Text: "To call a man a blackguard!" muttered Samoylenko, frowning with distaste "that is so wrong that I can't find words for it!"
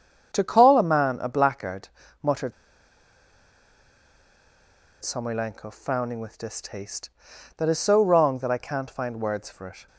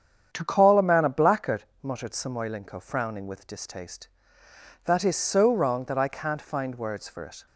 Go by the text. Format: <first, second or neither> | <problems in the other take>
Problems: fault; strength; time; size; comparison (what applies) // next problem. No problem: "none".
second | starts louder than the rest; strong; until 1.3 s; 7.5 dB; strong in the second // pauses between "muttered" and "Samoylenko"; strong; at 2.5 s; 2.4 s long